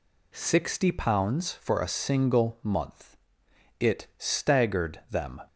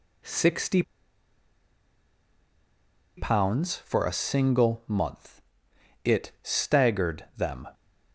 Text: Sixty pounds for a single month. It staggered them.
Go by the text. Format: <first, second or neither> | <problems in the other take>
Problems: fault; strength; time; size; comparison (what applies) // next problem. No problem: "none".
first | pauses between "Sixty" and "pounds"; strong; at 0.8 s; 2.3 s long